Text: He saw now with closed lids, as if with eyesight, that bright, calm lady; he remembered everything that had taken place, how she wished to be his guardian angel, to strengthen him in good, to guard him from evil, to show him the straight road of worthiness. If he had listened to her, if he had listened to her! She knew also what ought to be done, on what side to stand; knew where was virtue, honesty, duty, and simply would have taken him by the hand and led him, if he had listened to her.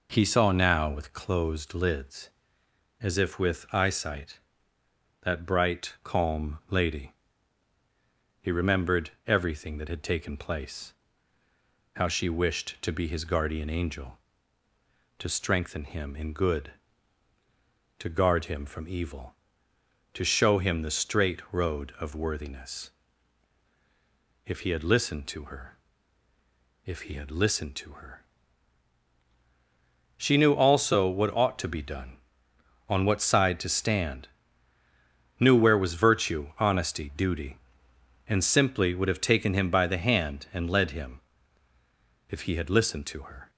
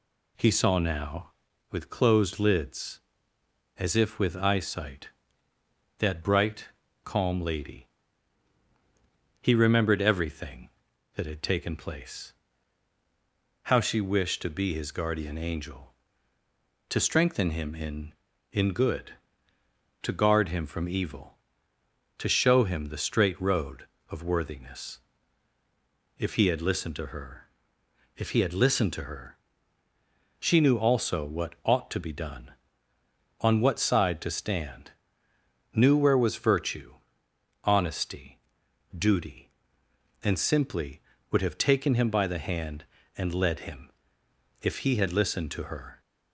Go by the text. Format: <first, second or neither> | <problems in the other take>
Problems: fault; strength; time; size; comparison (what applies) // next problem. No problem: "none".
first | says "in" twice; at 18.5 s